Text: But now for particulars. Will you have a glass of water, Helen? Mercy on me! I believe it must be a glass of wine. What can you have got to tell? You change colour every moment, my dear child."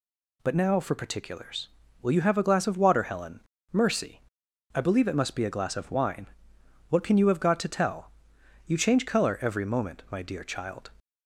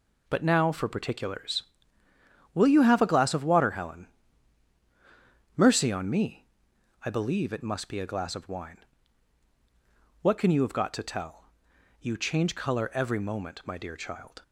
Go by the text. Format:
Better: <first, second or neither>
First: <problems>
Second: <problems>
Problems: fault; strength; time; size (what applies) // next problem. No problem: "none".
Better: second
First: skips "on me"; at 4.4 s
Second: none